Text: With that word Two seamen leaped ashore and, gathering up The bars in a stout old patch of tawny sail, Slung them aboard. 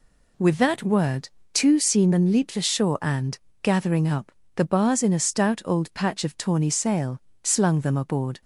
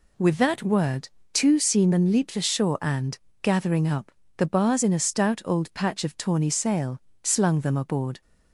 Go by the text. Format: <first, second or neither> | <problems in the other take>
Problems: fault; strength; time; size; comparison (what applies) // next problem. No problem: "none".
neither | pauses between "word" and "Two"; slight; the same in both // pauses between "up" and "The"; slight; the same in both